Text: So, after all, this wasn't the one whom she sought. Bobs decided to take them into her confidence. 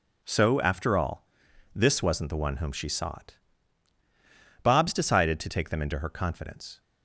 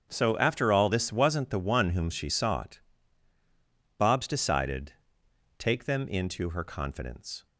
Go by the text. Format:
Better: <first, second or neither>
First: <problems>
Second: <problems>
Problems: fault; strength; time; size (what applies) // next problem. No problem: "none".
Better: first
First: none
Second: starts louder than the rest; strong; until 1.1 s; 7.5 dB // skips "to"; at 5.2 s